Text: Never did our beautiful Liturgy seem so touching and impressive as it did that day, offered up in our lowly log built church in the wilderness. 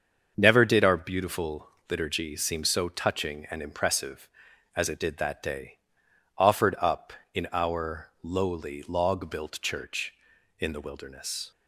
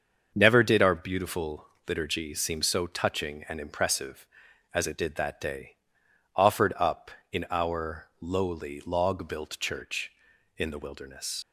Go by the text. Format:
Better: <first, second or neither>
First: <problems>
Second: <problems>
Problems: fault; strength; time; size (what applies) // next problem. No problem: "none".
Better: first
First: starts louder than the rest; until 1.3 s; 6.5 dB // pauses between "beautiful" and "Liturgy"; slight; at 1.6 s; 0.20 s long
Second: starts louder than the rest; until 1.3 s; 6.5 dB // pauses between "beautiful" and "Liturgy"; slight; at 1.6 s; 0.20 s long // leaves "wilderness" unfinished; at 11.4 s; 65 ms